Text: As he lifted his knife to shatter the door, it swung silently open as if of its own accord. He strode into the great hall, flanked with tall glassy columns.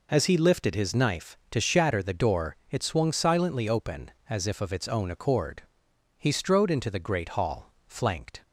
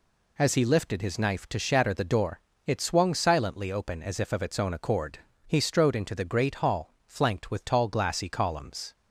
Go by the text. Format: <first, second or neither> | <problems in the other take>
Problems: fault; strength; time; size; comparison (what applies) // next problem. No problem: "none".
second | stops before "with tall glassy columns"; at 8.4 s